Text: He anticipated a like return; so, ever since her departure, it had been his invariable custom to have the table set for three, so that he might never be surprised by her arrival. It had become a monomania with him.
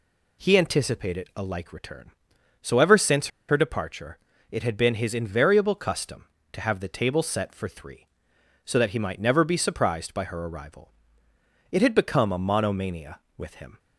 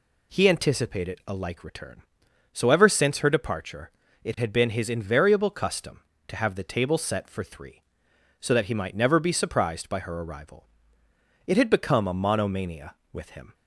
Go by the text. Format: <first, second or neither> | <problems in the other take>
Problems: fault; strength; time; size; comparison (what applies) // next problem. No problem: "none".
second | pauses between "since" and "her"; slight; at 3.2 s; 0.21 s long